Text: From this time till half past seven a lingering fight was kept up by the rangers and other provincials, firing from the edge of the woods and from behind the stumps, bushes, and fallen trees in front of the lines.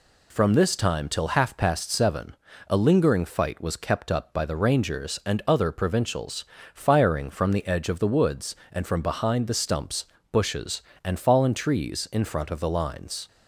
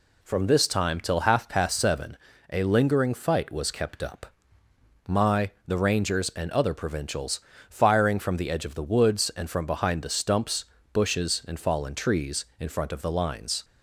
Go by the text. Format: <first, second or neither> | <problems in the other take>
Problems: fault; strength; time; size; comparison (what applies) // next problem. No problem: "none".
first | pauses between "seven" and "a"; slight; at 2.1 s; 0.34 s long; slight in the first // says "my" for "by"; at 5.0 s